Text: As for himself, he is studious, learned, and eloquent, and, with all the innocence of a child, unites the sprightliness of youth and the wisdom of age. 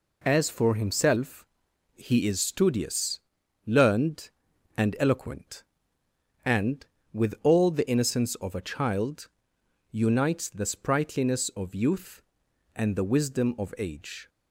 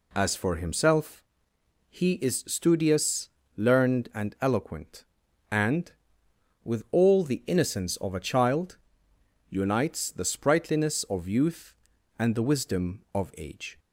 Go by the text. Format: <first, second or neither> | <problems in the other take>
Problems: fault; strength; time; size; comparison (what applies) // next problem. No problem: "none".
neither | none